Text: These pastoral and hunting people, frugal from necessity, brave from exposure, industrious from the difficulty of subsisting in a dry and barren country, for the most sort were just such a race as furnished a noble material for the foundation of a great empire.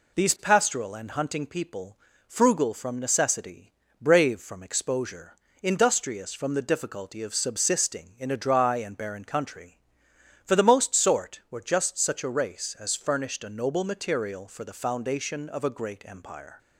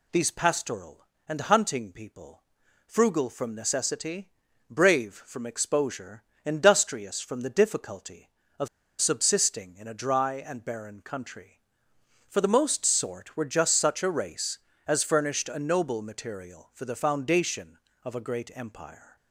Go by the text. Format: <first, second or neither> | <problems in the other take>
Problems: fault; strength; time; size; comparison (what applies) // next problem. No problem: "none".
first | pauses between "of" and "subsisting"; slight; at 8.6 s; 0.33 s long